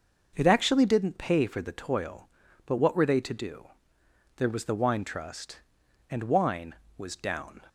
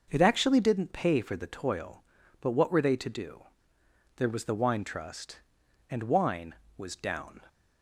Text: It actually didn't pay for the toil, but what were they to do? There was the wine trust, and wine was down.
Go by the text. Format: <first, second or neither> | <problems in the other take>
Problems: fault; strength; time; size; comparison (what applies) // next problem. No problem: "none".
neither | none